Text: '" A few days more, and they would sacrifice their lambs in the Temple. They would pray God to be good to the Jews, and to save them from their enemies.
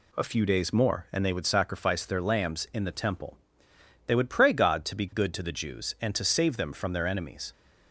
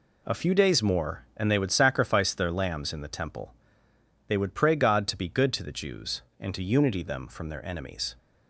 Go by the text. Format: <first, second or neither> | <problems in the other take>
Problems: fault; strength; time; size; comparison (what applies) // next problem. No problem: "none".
first | says "unity" for "save"; at 6.6 s